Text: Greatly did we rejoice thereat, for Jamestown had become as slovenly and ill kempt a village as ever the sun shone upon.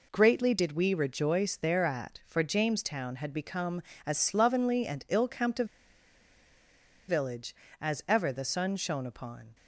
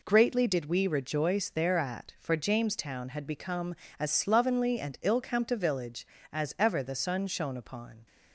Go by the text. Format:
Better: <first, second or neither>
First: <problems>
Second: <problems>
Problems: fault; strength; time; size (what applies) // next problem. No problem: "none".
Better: second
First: pauses between "a" and "village"; strong; at 5.6 s; 1.4 s long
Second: none